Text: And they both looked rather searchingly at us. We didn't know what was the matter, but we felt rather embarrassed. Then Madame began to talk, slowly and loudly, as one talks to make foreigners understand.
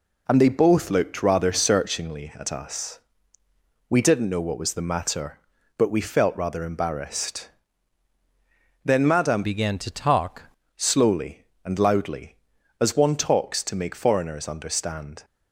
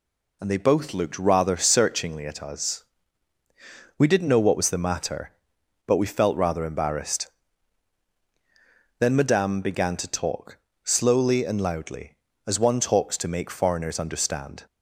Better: second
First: changes voice from "began" to "talk"; from 9.4 to 10.4 s; 1.0 s long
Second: none

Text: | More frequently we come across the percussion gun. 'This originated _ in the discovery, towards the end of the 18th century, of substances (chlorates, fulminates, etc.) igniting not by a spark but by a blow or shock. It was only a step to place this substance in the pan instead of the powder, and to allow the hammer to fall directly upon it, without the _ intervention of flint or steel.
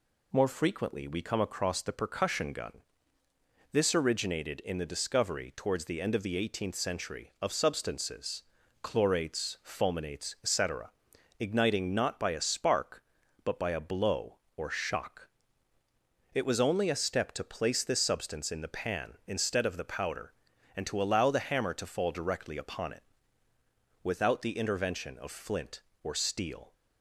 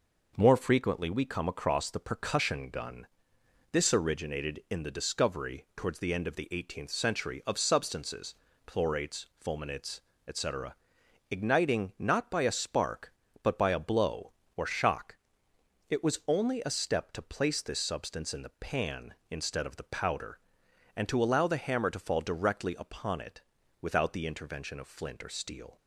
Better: neither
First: none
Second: none

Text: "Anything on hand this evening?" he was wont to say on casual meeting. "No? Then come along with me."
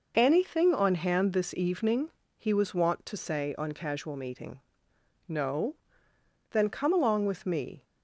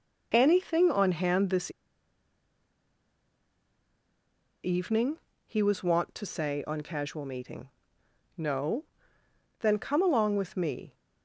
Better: first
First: none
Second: pauses between "this" and "evening"; strong; at 1.7 s; 2.9 s long

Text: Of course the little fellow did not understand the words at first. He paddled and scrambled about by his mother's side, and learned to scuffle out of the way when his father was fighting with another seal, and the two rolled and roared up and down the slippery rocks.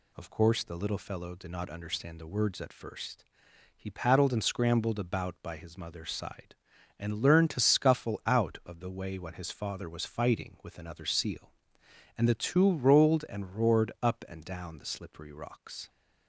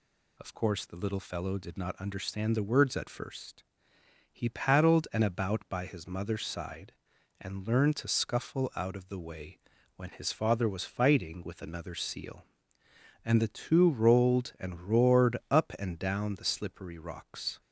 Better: first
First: none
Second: skips "scrambled"; at 5.2 s // pauses between "way" and "when"; at 9.5 s; 0.38 s long // pauses between "roared" and "up"; slight; at 15.3 s; 0.16 s long

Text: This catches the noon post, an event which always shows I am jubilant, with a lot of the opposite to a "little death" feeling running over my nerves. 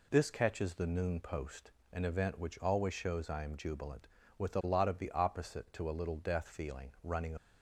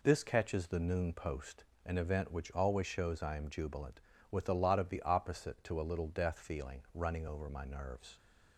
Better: second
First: stops before "over my nerves"; at 7.3 s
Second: none

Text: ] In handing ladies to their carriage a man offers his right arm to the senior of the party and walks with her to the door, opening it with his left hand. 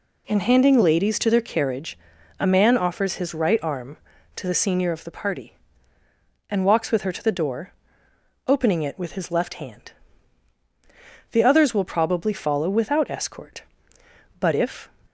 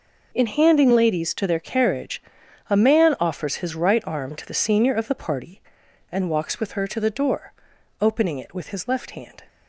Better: second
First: pauses between "carriage" and "a"; at 1.9 s; 0.40 s long // goes on to say "The others will probably follow without escort but if"; strong; from 11.3 s on; 3.5 s long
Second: pauses between "carriage" and "a"; noticeable; at 2.2 s; 0.48 s long

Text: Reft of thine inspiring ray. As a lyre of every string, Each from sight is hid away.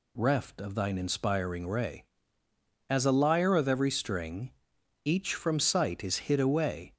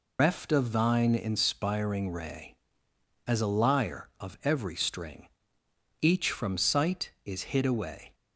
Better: first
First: none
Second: loses the start of "Reft"; at 0.1 s; 135 ms

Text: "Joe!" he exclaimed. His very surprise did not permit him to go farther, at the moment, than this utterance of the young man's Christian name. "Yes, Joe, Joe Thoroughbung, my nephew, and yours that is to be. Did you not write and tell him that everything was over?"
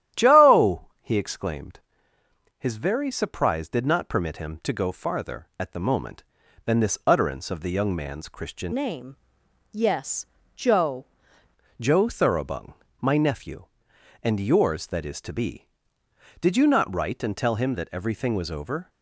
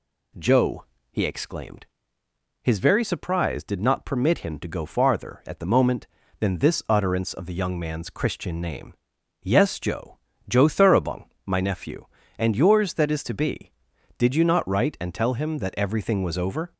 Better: second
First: starts louder than the rest; strong; until 1.2 s; 11.5 dB // changes voice from "name" to "Joe"; from 8.7 to 11.0 s; 2.3 s long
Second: none

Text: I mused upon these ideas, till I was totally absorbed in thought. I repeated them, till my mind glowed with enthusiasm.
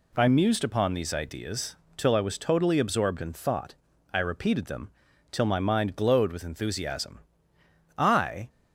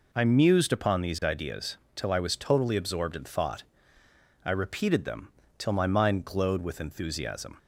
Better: second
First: goes on to say "I"; from 7.9 s on; 0.52 s long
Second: none

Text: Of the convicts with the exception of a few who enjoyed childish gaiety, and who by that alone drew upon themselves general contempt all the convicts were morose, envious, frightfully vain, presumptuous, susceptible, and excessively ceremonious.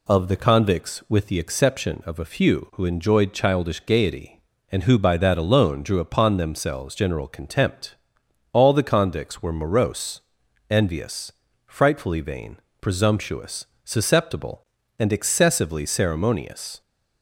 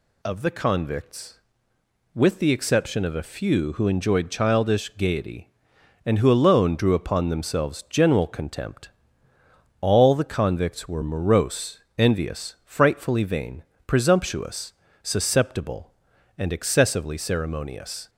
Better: first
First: pauses between "contempt" and "all"; noticeable; at 7.9 s; 0.56 s long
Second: skips "by that"; at 6.3 s // pauses between "contempt" and "all"; noticeable; at 8.9 s; 0.90 s long

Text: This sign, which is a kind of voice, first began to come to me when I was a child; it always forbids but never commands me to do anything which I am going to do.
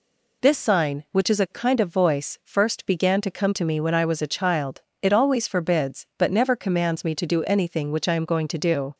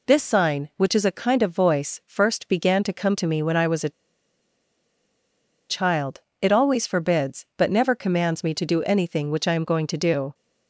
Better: first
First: none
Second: pauses between "a" and "child"; strong; at 3.9 s; 1.7 s long

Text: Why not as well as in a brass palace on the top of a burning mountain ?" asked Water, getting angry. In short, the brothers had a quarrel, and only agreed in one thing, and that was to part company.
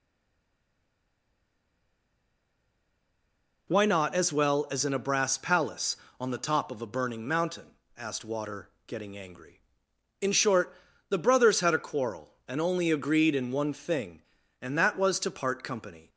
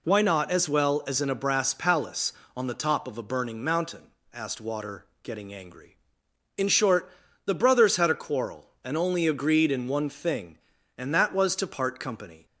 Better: second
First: stays silent before the first word; strong; until 3.6 s; 3.6 s long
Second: none

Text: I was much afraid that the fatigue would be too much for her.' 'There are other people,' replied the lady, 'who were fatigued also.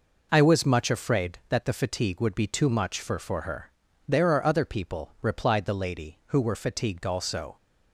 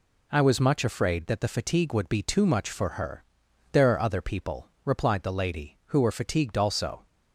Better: second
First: says "for" twice; at 3.1 s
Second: none

